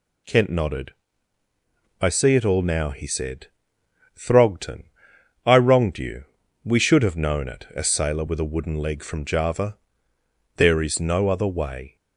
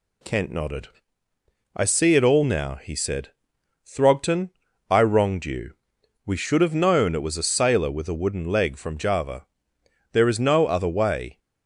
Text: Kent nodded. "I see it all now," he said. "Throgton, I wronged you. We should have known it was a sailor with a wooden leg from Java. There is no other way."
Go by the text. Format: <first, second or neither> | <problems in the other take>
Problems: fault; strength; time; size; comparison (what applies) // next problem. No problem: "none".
second | skips "was"; at 7.7 s